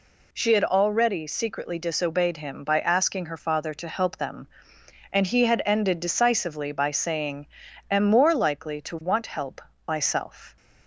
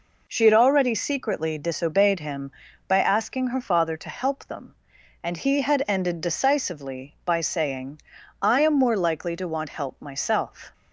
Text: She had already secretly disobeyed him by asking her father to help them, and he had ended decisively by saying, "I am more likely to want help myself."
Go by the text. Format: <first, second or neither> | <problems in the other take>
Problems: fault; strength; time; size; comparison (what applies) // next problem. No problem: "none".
second | skips "I"; at 7.6 s // pauses between "help" and "myself"; slight; at 9.6 s; 0.26 s long